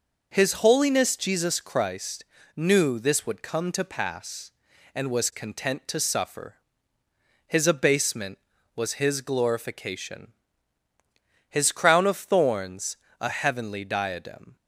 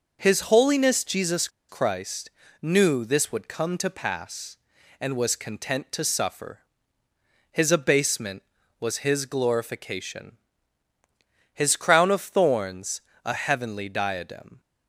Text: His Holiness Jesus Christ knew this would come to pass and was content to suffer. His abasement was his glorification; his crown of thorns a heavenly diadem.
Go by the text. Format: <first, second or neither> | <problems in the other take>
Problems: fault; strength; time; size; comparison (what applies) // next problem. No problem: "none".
first | pauses between "Jesus" and "Christ"; slight; at 1.4 s; 0.20 s long // pauses between "Christ" and "knew"; slight; at 2.2 s; 0.32 s long; slight in the first // pauses between "thorns" and "a"; slight; at 12.9 s; 0.26 s long; slight in the first